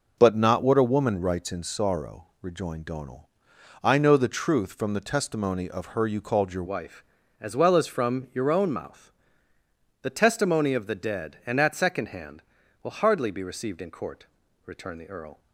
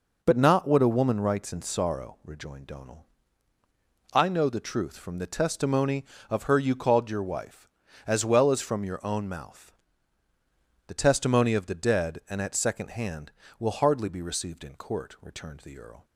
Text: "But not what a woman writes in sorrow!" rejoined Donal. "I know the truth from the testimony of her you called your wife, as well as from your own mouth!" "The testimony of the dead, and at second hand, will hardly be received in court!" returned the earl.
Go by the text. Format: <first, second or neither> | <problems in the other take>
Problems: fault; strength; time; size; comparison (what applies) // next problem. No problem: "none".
second | changes voice at "wife"; from 6.6 s on; 8.7 s long